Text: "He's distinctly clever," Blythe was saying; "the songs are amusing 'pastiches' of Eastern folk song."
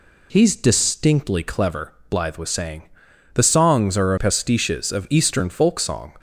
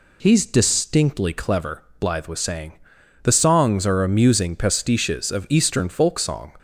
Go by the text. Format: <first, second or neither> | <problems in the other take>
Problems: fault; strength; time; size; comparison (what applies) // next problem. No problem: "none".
second | skips "amusing"; at 4.1 s